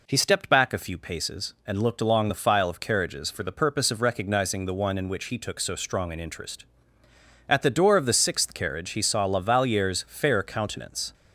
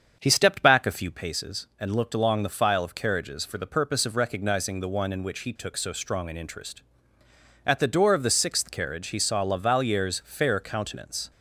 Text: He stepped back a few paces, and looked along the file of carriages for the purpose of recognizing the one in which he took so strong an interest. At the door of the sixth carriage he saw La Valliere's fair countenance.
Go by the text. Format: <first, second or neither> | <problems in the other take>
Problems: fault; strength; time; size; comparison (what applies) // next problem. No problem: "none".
first | starts louder than the rest; strong; until 1.4 s; 7.5 dB